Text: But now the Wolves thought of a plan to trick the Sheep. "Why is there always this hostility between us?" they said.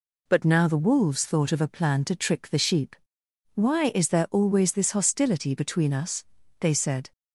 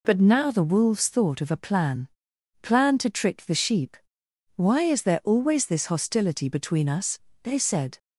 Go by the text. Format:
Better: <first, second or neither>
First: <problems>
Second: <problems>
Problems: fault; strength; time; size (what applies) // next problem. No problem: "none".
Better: first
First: none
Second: says "plan" twice; at 2.6 s